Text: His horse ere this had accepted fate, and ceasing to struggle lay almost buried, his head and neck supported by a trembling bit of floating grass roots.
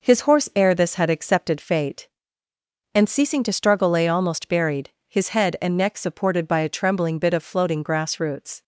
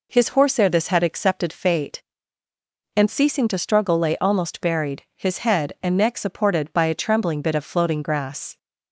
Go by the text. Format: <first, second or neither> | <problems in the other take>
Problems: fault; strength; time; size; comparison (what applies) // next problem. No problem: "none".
first | stops before "roots"; at 8.5 s